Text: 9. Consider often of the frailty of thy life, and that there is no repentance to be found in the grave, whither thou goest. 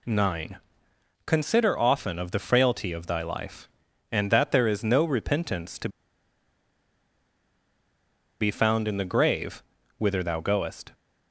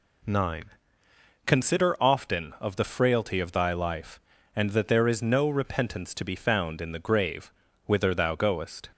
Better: second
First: pauses between "to" and "be"; strong; at 5.8 s; 2.5 s long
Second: none

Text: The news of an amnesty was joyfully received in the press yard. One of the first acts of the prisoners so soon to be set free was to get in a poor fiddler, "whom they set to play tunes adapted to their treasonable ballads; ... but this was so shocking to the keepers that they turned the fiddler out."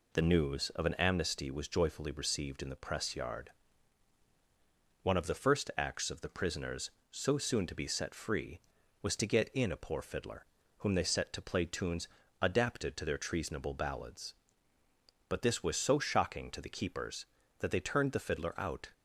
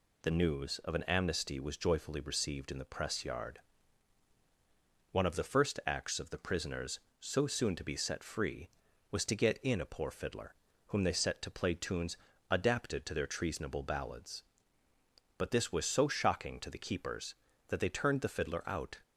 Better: second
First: starts louder than the rest; slight; until 1.2 s; 3 dB // pauses between "tunes" and "adapted"; slight; at 12.0 s; 0.32 s long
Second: pauses between "tunes" and "adapted"; slight; at 12.1 s; 0.32 s long

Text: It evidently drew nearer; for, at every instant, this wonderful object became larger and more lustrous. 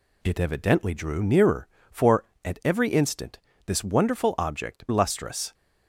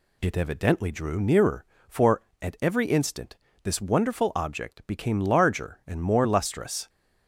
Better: second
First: skips "became larger and more"; at 4.8 s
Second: none

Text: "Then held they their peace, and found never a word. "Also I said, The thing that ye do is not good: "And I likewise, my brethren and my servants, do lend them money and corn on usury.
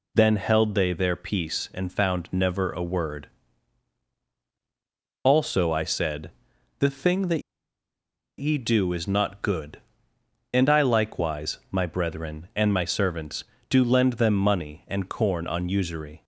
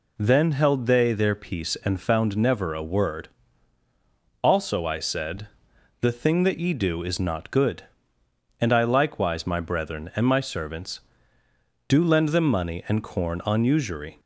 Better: second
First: pauses between "that" and "ye"; noticeable; at 7.4 s; 0.97 s long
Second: none

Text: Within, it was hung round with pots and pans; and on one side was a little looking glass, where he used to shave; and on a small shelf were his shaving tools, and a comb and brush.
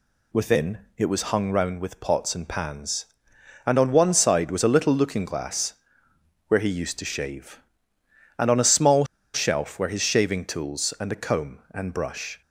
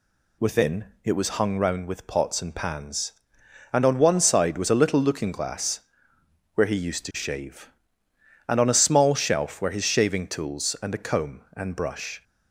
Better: second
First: pauses between "small" and "shelf"; slight; at 9.0 s; 0.30 s long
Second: none

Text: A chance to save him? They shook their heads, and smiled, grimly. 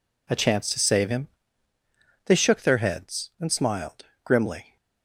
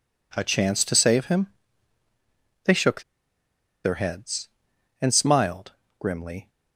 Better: first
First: none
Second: pauses between "shook" and "their"; noticeable; at 3.0 s; 0.82 s long

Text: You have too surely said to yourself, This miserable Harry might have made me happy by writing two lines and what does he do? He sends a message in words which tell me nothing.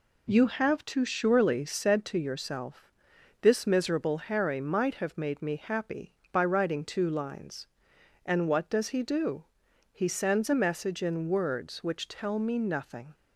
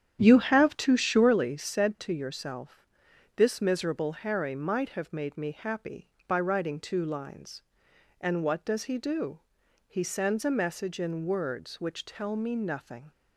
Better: first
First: none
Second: starts louder than the rest; strong; until 1.4 s; 9.5 dB

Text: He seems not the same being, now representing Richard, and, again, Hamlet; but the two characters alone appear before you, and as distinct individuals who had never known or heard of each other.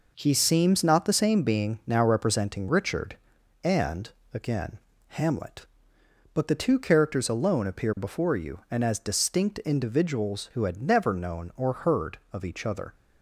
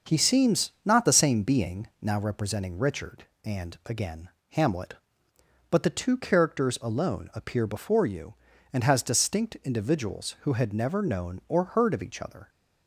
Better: first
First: none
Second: starts louder than the rest; noticeable; until 1.1 s; 6 dB // says "has" for "as"; at 8.8 s

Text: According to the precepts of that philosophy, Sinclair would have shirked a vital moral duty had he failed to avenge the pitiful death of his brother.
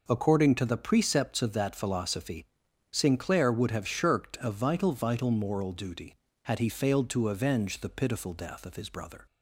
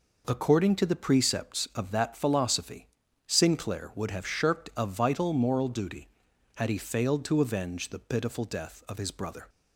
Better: second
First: says "vital" twice; at 4.9 s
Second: none

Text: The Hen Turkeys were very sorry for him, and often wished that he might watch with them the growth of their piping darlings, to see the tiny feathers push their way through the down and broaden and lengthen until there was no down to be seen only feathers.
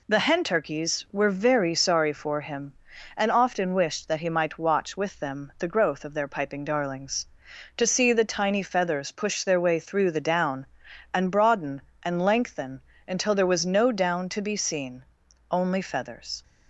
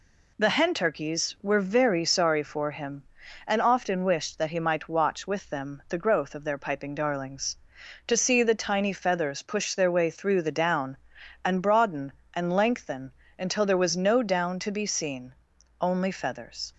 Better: neither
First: pauses between "lengthen" and "until"; slight; at 12.8 s; 0.26 s long // pauses between "seen" and "only"; noticeable; at 15.0 s; 0.48 s long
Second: pauses between "lengthen" and "until"; slight; at 13.1 s; 0.26 s long // pauses between "seen" and "only"; noticeable; at 15.3 s; 0.48 s long

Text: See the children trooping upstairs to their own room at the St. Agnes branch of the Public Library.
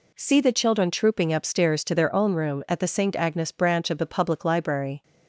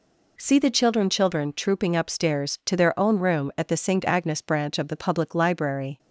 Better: first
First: none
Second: says "children" twice; at 1.0 s

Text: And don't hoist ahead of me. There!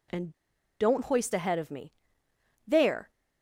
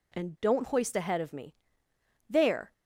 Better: second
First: pauses between "And" and "don't"; noticeable; at 0.3 s; 0.46 s long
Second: none

